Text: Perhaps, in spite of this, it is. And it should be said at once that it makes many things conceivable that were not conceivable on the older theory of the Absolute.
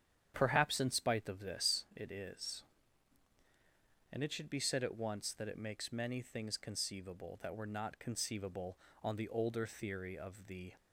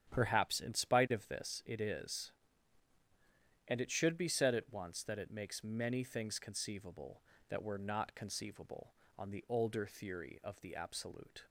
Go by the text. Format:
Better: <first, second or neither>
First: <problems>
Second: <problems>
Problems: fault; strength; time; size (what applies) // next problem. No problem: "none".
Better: second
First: starts louder than the rest; strong; until 1.3 s; 9 dB // stops before "Absolute"; at 10.7 s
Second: starts louder than the rest; strong; until 1.1 s; 10 dB